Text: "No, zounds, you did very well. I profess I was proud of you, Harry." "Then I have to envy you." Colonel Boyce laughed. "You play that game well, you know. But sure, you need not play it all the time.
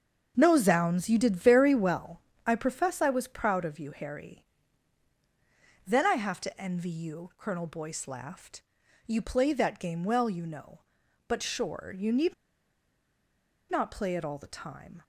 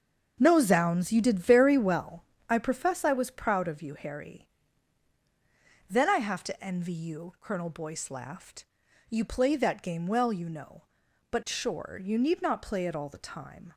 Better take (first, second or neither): second